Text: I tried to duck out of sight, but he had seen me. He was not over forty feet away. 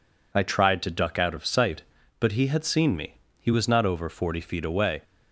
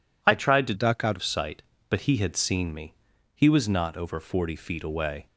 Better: first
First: none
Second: changes voice from "duck" to "of"; from 0.7 to 1.2 s; 0.5 s long

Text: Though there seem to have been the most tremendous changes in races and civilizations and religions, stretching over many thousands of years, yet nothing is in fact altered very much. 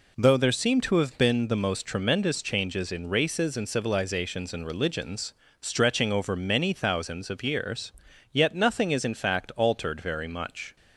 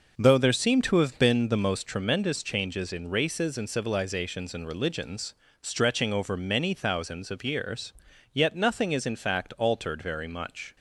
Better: first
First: none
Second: starts louder than the rest; noticeable; until 1.8 s; 5.5 dB

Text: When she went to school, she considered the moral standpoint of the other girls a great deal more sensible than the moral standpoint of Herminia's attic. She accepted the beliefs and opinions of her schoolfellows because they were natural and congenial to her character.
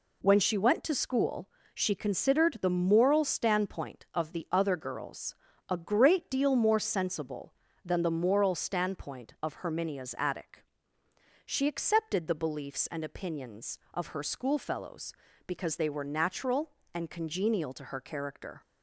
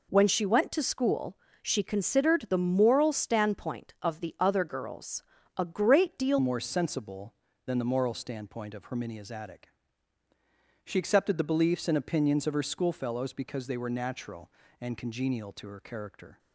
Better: first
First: pauses between "girls" and "a"; slight; at 5.3 s; 0.34 s long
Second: pauses between "girls" and "a"; slight; at 5.2 s; 0.34 s long // changes voice at "more"; from 6.3 s on; 10.0 s long

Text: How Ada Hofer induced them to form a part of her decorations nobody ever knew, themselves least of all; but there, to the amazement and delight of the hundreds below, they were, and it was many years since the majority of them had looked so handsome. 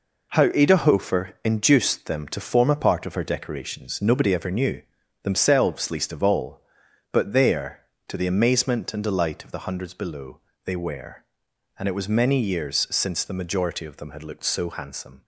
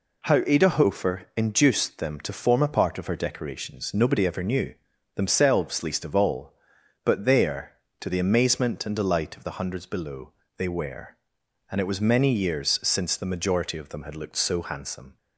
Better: second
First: gets quieter; strong; throughout; 7.5 dB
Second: none

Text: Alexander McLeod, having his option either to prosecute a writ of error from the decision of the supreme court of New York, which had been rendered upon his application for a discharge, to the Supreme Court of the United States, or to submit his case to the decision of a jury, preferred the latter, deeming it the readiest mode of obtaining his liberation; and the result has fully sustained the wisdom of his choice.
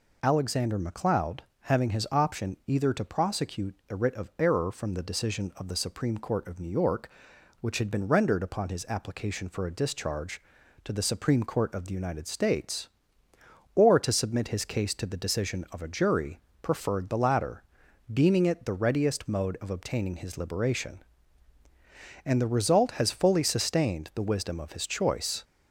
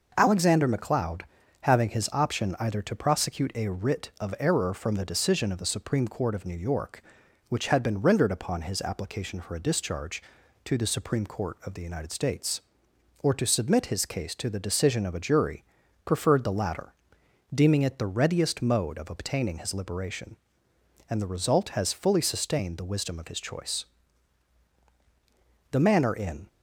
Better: first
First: none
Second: goes on to say "The manner in"; noticeable; from 25.7 s on; 0.76 s long

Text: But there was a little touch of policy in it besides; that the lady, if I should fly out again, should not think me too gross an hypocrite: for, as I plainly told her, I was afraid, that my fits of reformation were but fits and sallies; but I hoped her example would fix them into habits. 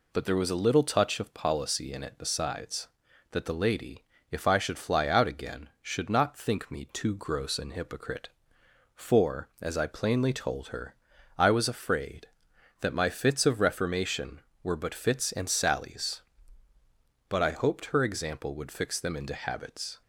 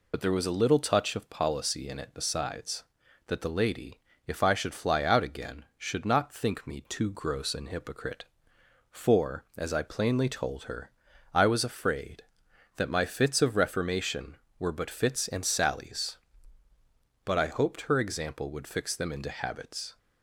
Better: first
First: none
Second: loses the start of "But"; at 0.1 s; 45 ms

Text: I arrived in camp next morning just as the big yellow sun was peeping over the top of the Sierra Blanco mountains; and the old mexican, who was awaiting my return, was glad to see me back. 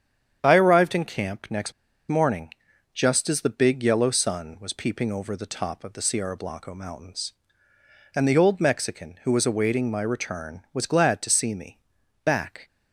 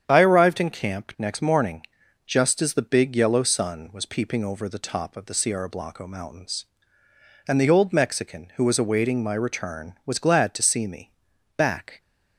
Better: second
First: starts louder than the rest; strong; until 1.4 s; 8.5 dB // pauses between "next" and "morning"; at 1.7 s; 0.37 s long // pauses between "morning" and "just"; at 2.5 s; 0.42 s long // pauses between "me" and "back"; noticeable; at 11.7 s; 0.46 s long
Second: starts louder than the rest; strong; until 1.0 s; 8.5 dB // pauses between "morning" and "just"; at 1.8 s; 0.42 s long // pauses between "me" and "back"; noticeable; at 11.1 s; 0.46 s long

